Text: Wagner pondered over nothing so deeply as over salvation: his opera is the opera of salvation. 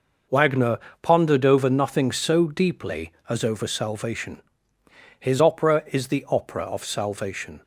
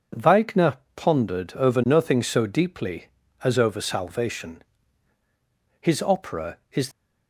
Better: first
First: pauses between "Wagner" and "pondered"; slight; at 0.7 s; 0.24 s long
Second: pauses between "Wagner" and "pondered"; slight; at 0.7 s; 0.18 s long // stops before "the opera of salvation"; at 6.9 s

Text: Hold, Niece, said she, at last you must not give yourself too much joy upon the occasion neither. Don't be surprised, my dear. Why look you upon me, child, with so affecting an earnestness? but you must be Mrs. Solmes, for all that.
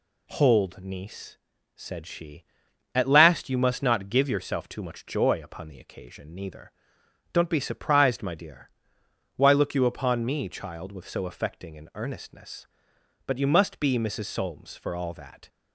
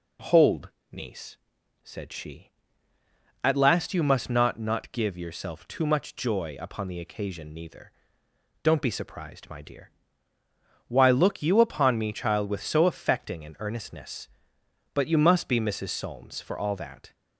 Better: first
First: none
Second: says "not" twice; at 4.5 s

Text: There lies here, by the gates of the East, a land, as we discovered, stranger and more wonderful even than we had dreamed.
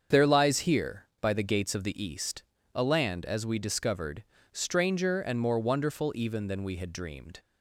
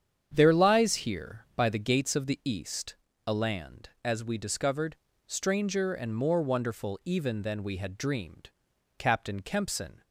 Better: first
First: starts louder than the rest; strong; until 1.2 s; 7.5 dB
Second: starts louder than the rest; strong; until 1.3 s; 8 dB // goes on to say "Captain Kempson"; noticeable; from 8.9 s on; 1.0 s long

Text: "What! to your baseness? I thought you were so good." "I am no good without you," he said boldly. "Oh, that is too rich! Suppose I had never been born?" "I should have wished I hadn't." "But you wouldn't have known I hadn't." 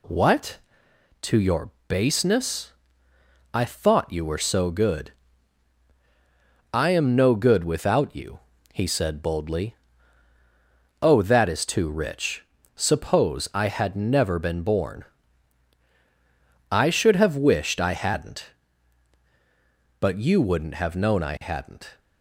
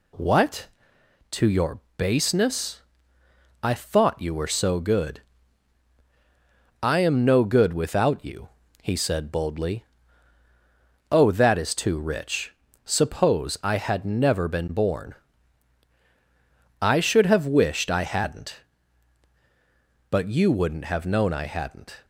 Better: neither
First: pauses between "your" and "baseness"; slight; at 1.7 s; 0.16 s long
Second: pauses between "your" and "baseness"; slight; at 1.8 s; 0.16 s long

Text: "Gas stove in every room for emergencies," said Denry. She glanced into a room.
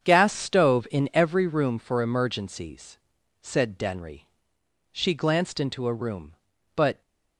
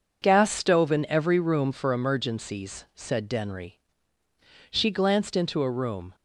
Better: second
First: starts louder than the rest; strong; until 1.0 s; 7.5 dB // goes on to say "But"; slight; from 6.7 s on; 0.26 s long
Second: none

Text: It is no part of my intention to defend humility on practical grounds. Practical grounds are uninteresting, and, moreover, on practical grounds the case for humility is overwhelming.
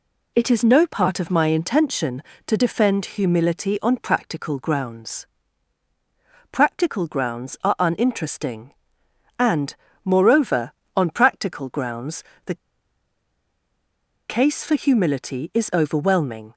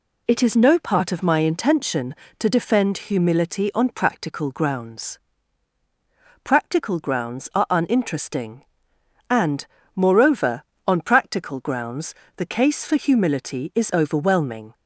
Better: second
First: pauses between "grounds" and "the"; slight; at 12.2 s; 0.22 s long // pauses between "the" and "case"; strong; at 12.5 s; 1.7 s long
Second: pauses between "grounds" and "the"; slight; at 12.1 s; 0.22 s long

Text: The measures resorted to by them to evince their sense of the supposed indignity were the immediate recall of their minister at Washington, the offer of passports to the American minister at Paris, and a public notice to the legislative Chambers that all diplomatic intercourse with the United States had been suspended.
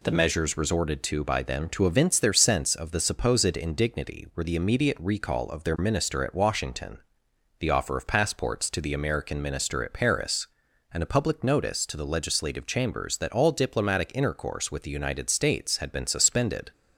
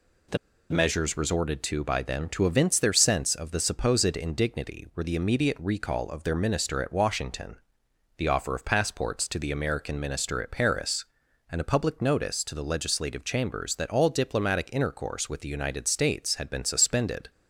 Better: first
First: none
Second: pauses between "The" and "measures"; slight; at 0.3 s; 0.32 s long

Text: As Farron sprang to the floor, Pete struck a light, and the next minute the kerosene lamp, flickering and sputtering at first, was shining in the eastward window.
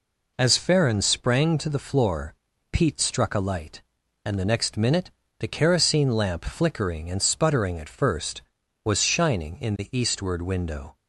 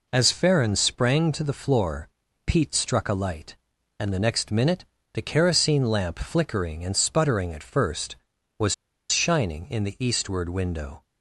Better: first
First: pauses between "minute" and "the"; slight; at 5.1 s; 0.26 s long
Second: pauses between "minute" and "the"; slight; at 4.8 s; 0.26 s long // pauses between "was" and "shining"; slight; at 8.7 s; 0.35 s long

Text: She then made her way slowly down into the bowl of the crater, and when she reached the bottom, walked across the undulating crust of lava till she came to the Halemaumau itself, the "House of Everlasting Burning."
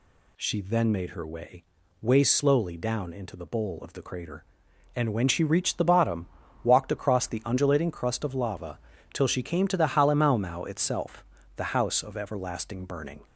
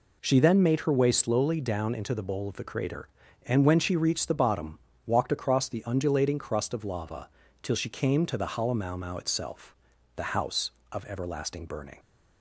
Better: second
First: says "way" twice; at 2.0 s // pauses between "lava" and "till"; slight; at 8.7 s; 0.34 s long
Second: pauses between "lava" and "till"; slight; at 7.2 s; 0.34 s long

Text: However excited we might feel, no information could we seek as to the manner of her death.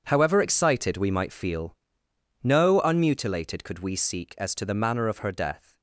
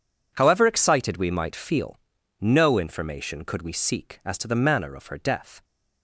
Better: second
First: says "unmutilated" for "information"; at 2.8 s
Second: none

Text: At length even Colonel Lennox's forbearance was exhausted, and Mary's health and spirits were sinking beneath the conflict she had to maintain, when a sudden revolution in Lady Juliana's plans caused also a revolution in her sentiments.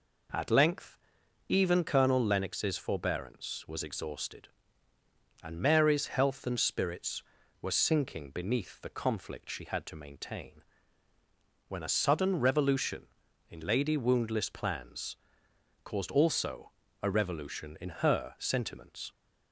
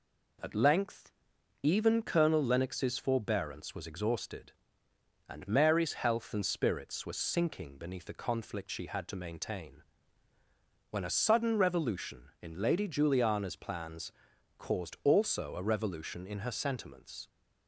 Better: second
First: pauses between "length" and "even"; noticeable; at 0.9 s; 0.52 s long // says "Woundless" for "Juliana's"; at 13.9 s // pauses between "plans" and "caused"; noticeable; at 15.1 s; 0.66 s long // pauses between "also" and "a"; slight; at 16.7 s; 0.32 s long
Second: pauses between "length" and "even"; noticeable; at 1.1 s; 0.50 s long // pauses between "plans" and "caused"; at 14.1 s; 0.44 s long

